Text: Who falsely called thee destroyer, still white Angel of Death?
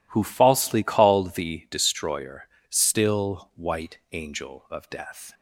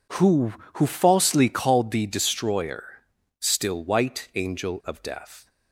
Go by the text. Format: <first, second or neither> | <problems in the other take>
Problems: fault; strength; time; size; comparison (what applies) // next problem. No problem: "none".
first | says "Who" twice; at 0.7 s